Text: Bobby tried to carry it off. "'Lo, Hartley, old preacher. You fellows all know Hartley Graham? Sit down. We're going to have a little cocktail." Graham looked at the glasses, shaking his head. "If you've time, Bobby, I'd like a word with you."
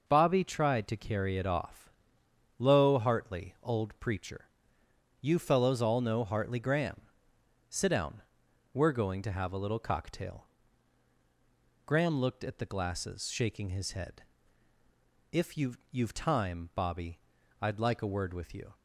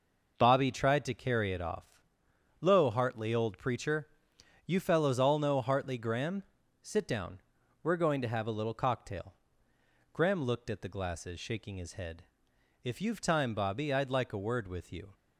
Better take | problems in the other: second | says "you've" twice; at 15.9 s

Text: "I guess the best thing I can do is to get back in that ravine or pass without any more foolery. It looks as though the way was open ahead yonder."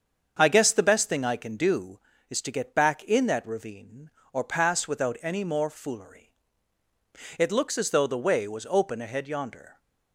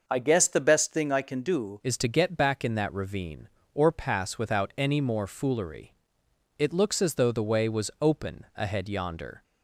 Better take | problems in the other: first | starts louder than the rest; until 1.0 s; 6 dB; also in the first // changes voice at "is"; from 1.8 s on; 7.6 s long

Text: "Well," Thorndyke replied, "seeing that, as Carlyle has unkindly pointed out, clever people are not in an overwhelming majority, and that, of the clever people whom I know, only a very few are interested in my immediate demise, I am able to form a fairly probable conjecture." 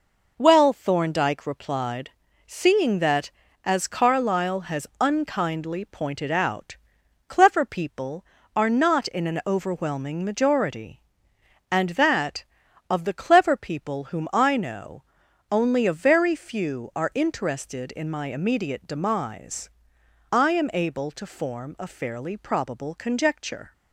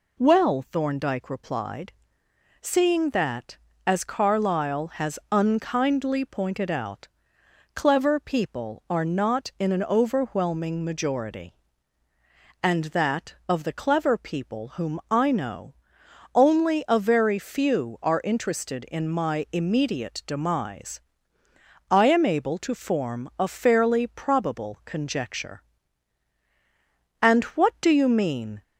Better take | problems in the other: first | goes on to say "And what do you mean"; from 27.2 s on; 1.4 s long

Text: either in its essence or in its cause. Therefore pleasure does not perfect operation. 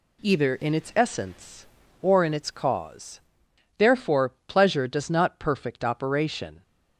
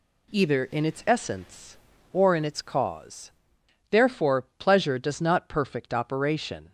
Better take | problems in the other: neither | none

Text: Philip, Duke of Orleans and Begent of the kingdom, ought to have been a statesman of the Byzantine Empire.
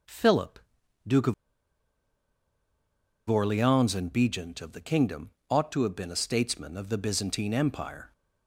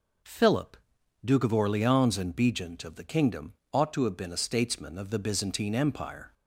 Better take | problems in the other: second | pauses between "of" and "Orleans"; strong; at 1.3 s; 1.9 s long

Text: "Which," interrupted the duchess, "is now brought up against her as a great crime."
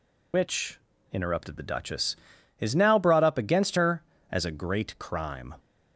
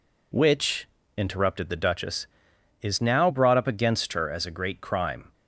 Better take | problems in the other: second | loses the start of "Which"; at 0.3 s; 55 ms

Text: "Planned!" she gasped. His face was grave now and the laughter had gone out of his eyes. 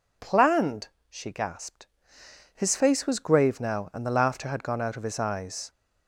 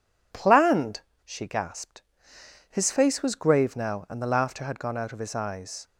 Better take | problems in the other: second | gets louder; throughout; 3.5 dB

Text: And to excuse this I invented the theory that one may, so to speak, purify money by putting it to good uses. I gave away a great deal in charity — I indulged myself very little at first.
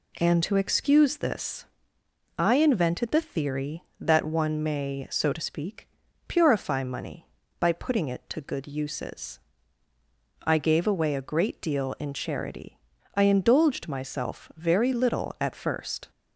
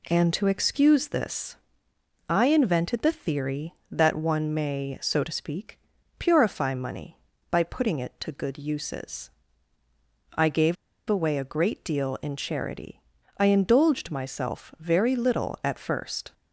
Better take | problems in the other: first | pauses between "this" and "I"; noticeable; at 1.5 s; 0.72 s long; noticeable in the first // pauses between "gave" and "away"; slight; at 10.7 s; 0.33 s long

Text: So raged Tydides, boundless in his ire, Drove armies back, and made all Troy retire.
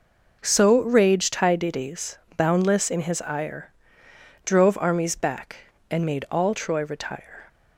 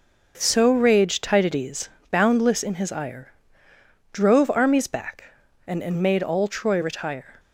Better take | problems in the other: first | says "and" twice; at 5.8 s

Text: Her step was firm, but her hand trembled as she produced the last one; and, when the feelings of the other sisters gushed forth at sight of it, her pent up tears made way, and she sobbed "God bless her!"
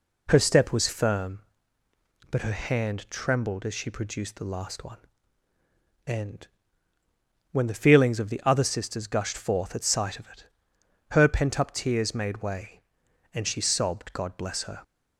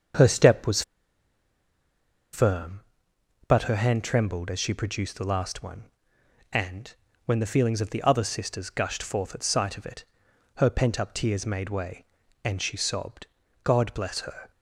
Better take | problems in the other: first | starts louder than the rest; until 2.6 s; 7 dB // pauses between "was" and "firm"; strong; at 0.8 s; 1.5 s long // pauses between "sobbed" and "God"; at 13.2 s; 0.38 s long

